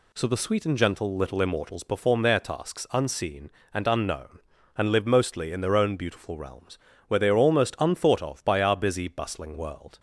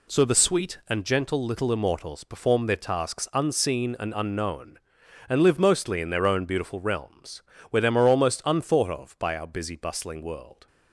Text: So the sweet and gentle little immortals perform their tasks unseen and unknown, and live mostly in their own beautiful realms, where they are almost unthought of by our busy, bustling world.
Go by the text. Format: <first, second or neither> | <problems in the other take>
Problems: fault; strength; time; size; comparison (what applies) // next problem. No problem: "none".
first | says "them" for "they"; at 7.8 s